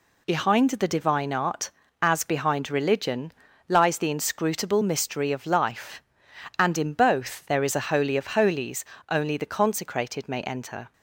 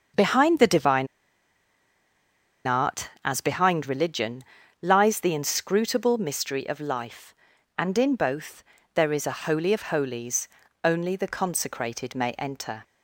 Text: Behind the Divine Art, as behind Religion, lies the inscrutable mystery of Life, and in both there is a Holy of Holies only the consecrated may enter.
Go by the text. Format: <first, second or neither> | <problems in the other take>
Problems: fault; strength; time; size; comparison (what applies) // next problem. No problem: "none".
first | starts louder than the rest; until 2.7 s; 6.5 dB // pauses between "Divine" and "Art"; strong; at 1.0 s; 1.6 s long // pauses between "both" and "there"; slight; at 8.6 s; 0.30 s long // pauses between "Holies" and "only"; slight; at 10.4 s; 0.36 s long; slight in the first